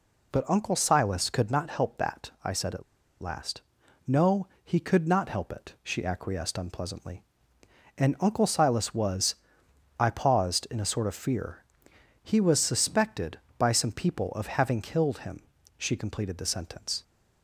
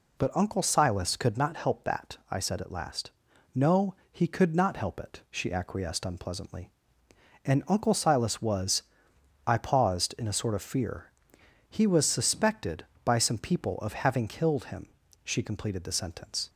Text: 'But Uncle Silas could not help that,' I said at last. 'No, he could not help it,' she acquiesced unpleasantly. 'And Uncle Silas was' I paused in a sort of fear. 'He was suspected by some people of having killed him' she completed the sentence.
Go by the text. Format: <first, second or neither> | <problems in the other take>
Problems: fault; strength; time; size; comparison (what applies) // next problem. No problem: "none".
second | pauses between "at" and "last"; at 2.8 s; 0.39 s long // pauses between "was" and "I"; noticeable; at 9.3 s; 0.64 s long; noticeable in the second // pauses between "him" and "she"; slight; at 15.4 s; 0.34 s long; slight in the second